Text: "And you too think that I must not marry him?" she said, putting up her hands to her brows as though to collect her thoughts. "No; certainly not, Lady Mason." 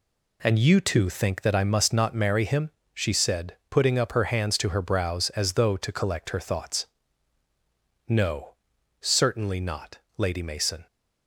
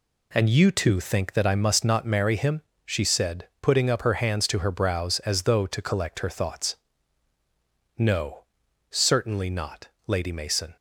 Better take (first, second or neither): neither